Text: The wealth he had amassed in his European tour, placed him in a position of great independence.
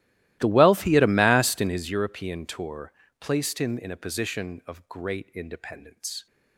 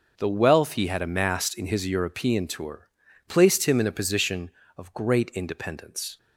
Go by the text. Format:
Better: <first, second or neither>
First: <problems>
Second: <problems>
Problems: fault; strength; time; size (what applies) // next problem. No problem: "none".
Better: second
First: starts louder than the rest; strong; until 2.0 s; 16 dB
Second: none